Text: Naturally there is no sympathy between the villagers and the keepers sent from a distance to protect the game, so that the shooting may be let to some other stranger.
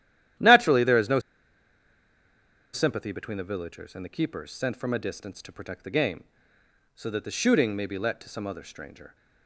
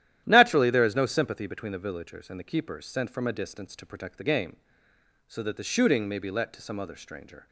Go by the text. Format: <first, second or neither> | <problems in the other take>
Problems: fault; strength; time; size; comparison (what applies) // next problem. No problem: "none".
second | starts louder than the rest; strong; until 2.9 s; 12 dB; strong in the second // pauses between "no" and "sympathy"; strong; at 1.1 s; 1.5 s long